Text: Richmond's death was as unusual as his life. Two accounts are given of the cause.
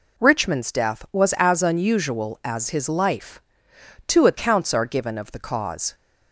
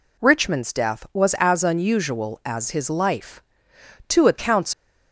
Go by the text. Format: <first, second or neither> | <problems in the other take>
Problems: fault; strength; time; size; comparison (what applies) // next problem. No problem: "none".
first | stops before "are given of the cause"; at 4.7 s